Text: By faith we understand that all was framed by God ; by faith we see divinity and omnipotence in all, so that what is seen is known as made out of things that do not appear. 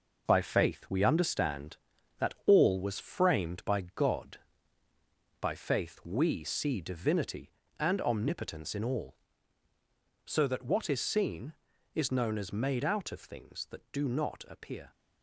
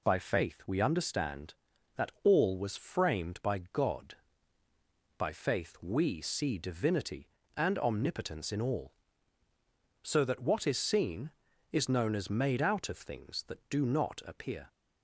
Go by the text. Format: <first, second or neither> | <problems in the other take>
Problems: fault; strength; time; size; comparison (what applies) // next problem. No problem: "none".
second | gets quieter; throughout; 7 dB